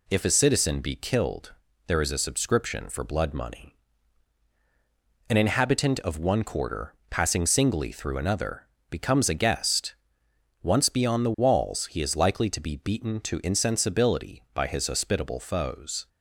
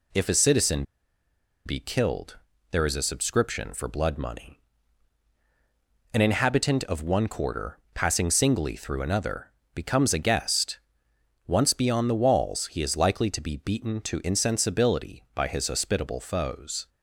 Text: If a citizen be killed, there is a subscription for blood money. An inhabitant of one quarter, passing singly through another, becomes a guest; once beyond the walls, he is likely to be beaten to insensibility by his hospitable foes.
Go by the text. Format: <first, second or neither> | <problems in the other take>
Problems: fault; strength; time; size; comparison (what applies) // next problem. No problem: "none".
first | pauses between "citizen" and "be"; noticeable; at 0.8 s; 0.83 s long